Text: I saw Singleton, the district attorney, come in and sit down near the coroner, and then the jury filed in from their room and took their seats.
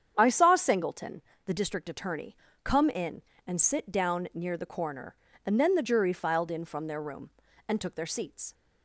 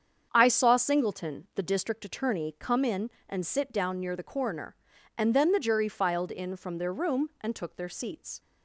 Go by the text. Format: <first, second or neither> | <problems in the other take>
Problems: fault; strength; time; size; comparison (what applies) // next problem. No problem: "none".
neither | starts louder than the rest; strong; the same in both